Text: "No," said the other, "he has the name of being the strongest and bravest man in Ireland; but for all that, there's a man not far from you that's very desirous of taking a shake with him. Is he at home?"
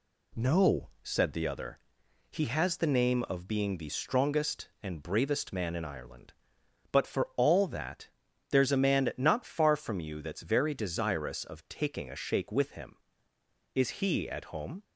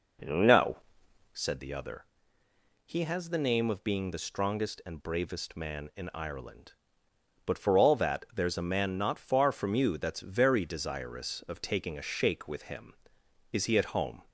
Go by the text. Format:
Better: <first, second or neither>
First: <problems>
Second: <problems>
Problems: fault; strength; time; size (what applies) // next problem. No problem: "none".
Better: first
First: none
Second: starts louder than the rest; noticeable; until 1.5 s; 5 dB